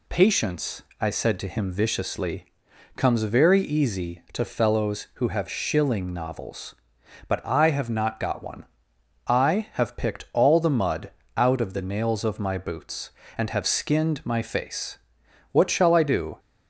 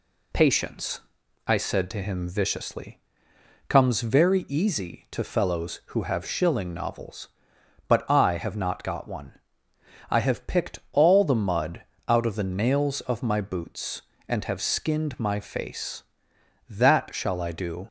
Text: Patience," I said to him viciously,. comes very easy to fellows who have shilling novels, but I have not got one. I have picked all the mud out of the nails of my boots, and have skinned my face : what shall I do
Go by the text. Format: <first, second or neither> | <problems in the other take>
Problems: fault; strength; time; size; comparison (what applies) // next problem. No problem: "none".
first | pauses between "mud" and "out"; slight; at 11.8 s; 0.24 s long; slight in the first // says "that" for "what"; at 16.7 s